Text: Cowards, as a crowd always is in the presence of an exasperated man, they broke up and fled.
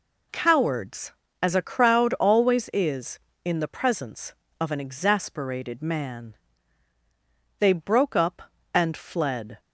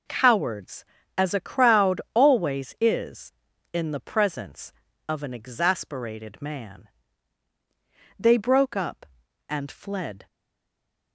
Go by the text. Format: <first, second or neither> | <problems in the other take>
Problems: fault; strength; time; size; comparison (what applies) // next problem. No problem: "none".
first | stays silent after the last word; slight; from 10.2 s on; 0.9 s long